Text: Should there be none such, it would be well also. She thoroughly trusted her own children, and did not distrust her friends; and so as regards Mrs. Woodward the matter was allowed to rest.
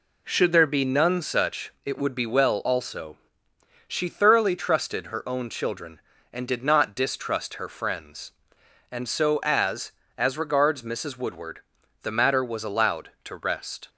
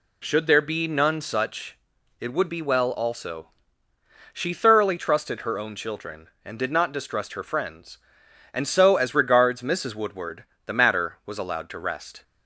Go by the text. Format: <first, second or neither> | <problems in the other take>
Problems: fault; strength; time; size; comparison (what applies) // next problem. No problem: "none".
second | says "as" twice; at 10.1 s // pauses between "Woodward" and "the"; at 11.5 s; 0.44 s long; slight in the second